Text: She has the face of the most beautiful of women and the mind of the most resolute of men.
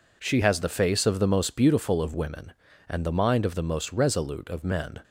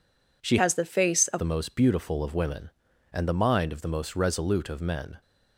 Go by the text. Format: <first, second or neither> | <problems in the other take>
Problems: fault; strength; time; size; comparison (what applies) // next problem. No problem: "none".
first | changes voice from "has" to "of"; from 0.5 to 1.4 s; 0.9 s long